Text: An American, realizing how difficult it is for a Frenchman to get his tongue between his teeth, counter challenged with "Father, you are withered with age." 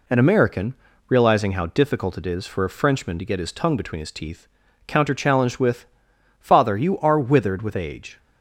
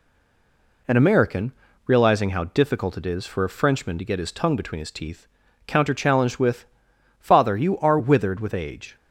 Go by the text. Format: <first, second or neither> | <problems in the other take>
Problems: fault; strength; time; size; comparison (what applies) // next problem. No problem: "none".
first | stays silent before the first word; slight; until 0.8 s; 0.8 s long // pauses between "with" and "Father"; noticeable; at 6.6 s; 0.54 s long; noticeable in the first